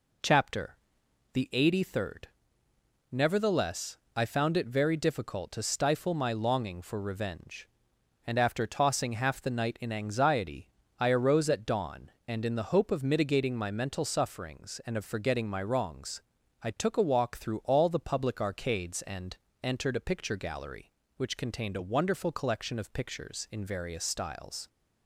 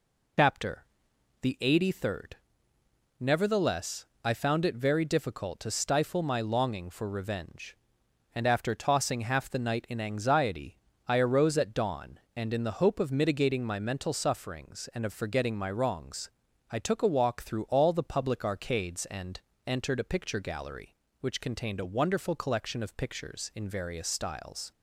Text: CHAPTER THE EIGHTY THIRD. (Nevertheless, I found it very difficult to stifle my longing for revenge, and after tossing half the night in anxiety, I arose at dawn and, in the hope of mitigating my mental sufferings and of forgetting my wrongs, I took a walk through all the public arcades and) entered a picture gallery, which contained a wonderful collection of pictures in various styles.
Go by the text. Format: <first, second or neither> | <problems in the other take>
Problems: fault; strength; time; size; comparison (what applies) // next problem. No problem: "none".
first | loses the start of "CHAPTER"; at 0.3 s; 65 ms // pauses between "CHAPTER" and "THE"; noticeable; at 0.8 s; 0.58 s long; noticeable in the first